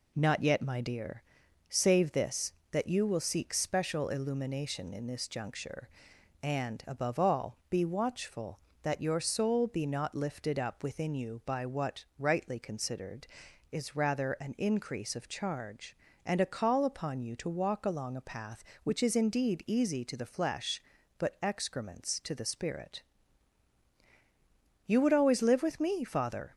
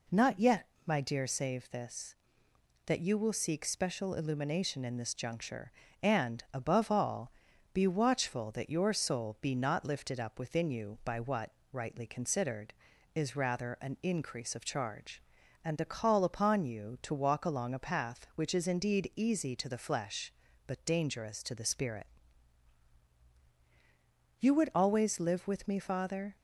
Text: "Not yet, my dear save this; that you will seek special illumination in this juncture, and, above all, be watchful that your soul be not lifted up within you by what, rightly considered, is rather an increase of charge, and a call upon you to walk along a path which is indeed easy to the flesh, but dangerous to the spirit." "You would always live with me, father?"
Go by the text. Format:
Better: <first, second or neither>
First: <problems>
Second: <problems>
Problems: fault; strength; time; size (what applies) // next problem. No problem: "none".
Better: second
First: pauses between "dear" and "save"; noticeable; at 1.2 s; 0.46 s long // says "excrements" for "dangerous"; at 21.4 s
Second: none